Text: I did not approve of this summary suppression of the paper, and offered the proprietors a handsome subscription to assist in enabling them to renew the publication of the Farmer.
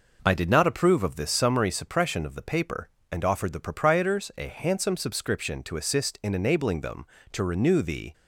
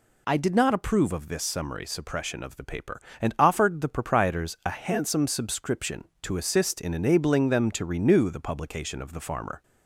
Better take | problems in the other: second | stops before "publication of the Farmer"; at 8.1 s

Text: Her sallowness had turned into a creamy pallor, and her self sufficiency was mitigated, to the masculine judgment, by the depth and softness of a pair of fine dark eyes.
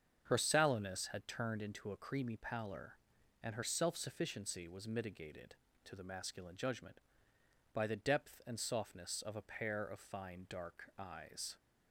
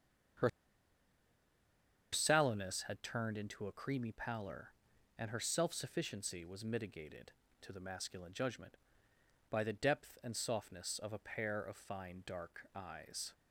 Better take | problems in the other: first | starts louder than the rest; strong; until 3.0 s; 7 dB; strong in the first // pauses between "Her" and "sallowness"; strong; at 0.4 s; 1.6 s long

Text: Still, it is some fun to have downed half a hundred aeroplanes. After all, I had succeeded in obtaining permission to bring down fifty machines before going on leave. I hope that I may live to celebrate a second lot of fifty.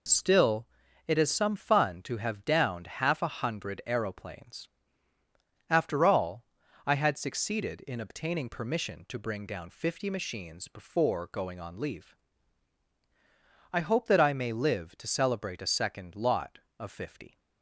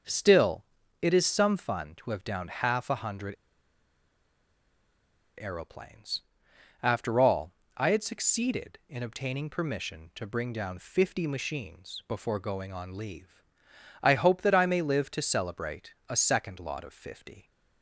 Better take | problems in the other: first | starts louder than the rest; until 1.4 s; 6.5 dB // pauses between "hundred" and "aeroplanes"; strong; at 3.3 s; 2.0 s long // pauses between "celebrate" and "a"; slight; at 15.9 s; 0.16 s long

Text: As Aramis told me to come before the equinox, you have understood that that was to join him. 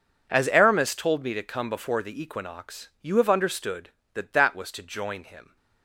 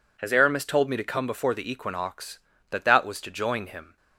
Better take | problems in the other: first | skips "you have understood"; at 2.5 s

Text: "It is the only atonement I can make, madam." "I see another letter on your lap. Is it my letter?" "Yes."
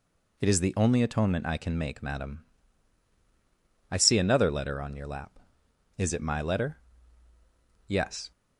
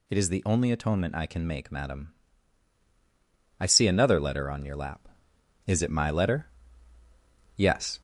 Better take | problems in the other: first | gets louder; slight; throughout; 3 dB

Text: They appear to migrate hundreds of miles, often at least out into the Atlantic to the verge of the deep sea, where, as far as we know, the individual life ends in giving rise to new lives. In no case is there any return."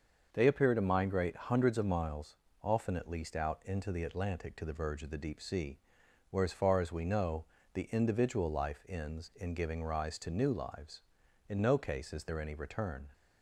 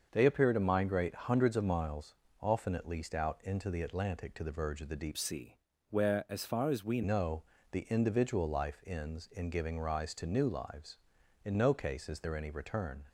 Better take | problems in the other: first | starts louder than the rest; until 1.1 s; 6.5 dB; also in the first // changes voice from "sea" to "we"; from 5.1 to 7.0 s; 1.9 s long

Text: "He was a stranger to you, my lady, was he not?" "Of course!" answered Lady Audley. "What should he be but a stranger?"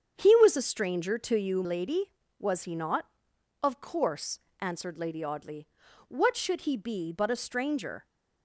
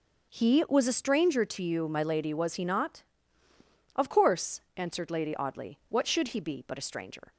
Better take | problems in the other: second | starts louder than the rest; strong; until 1.1 s; 7.5 dB; also in the second // skips "my"; at 1.6 s

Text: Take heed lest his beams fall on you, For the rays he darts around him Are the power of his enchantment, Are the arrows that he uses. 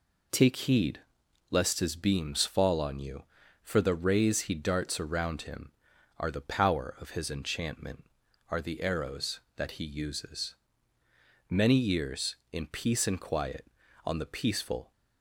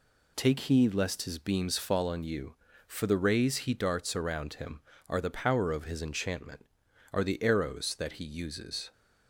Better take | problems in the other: second | pauses between "heed" and "lest"; noticeable; at 0.9 s; 0.50 s long // goes on to say "Many years in peace and quiet On the peaceful"; strong; from 11.4 s on; 3.4 s long

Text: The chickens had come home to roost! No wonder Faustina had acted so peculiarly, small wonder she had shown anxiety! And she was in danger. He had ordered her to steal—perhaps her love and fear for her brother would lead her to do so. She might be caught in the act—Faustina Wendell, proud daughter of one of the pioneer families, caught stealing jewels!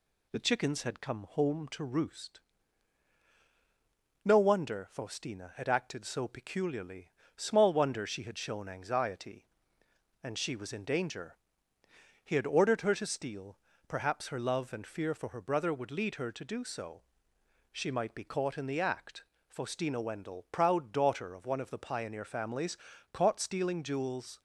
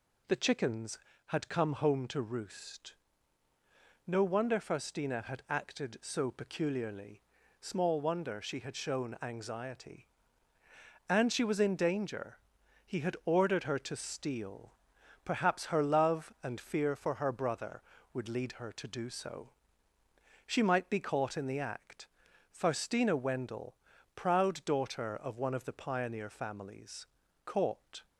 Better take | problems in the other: first | stops before "stealing jewels"; at 28.0 s

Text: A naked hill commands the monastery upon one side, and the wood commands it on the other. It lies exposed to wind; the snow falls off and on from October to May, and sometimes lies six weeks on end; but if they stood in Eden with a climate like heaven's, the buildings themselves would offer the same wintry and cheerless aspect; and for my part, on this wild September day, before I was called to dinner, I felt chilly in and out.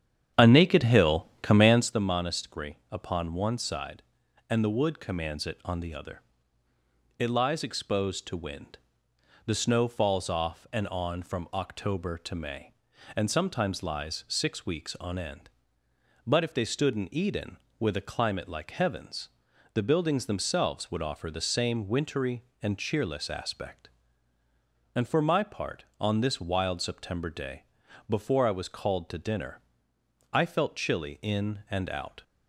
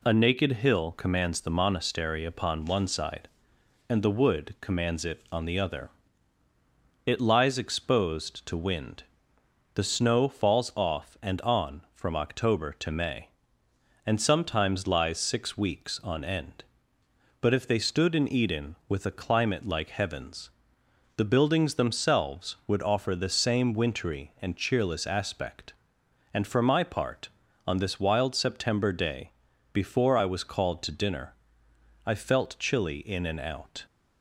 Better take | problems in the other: second | starts louder than the rest; strong; until 2.0 s; 9 dB

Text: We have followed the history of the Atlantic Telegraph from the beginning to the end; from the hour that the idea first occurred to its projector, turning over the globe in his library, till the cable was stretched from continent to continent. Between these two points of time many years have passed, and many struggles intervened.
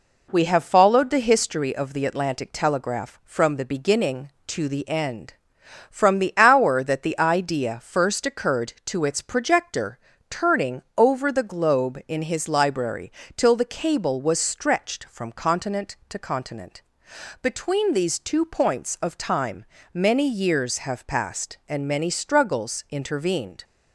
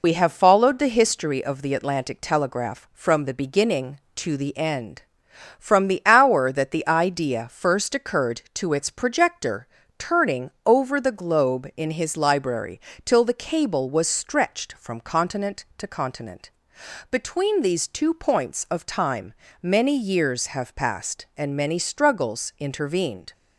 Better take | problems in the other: first | loses the start of "We"; at 0.0 s; 60 ms // pauses between "time" and "many"; slight; at 19.3 s; 0.30 s long; slight in the first

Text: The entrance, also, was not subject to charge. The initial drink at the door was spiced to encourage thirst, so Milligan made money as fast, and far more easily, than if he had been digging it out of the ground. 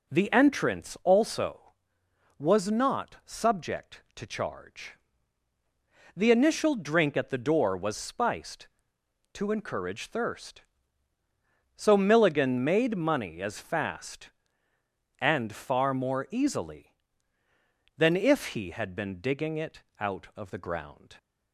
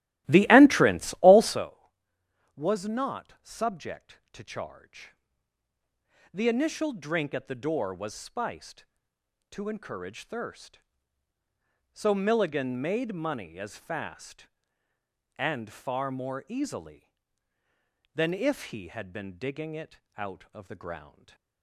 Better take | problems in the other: first | starts louder than the rest; strong; until 1.6 s; 15.5 dB // pauses between "it" and "out"; slight; at 20.0 s; 0.16 s long; slight in the first // stays silent after the last word; slight; from 21.0 s on; 0.6 s long

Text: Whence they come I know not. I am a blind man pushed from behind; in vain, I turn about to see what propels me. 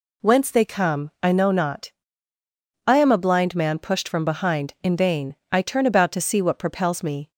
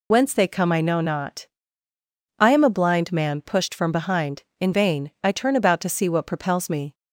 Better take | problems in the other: first | loses the start of "Whence"; at 0.1 s; 55 ms

